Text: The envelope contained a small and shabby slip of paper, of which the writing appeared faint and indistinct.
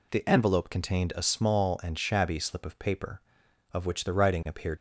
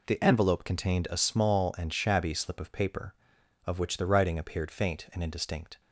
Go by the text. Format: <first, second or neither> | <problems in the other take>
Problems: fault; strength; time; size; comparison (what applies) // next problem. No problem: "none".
second | stops before "faint and indistinct"; at 4.7 s